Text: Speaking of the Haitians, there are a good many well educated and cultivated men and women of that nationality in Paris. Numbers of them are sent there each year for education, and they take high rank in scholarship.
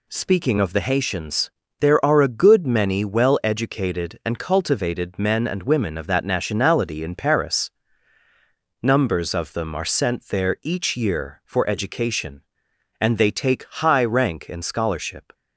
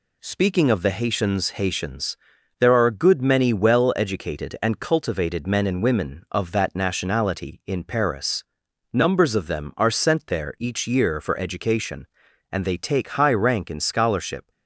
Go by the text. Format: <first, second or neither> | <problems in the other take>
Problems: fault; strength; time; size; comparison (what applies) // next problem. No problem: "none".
first | says "Haitians" twice; at 1.5 s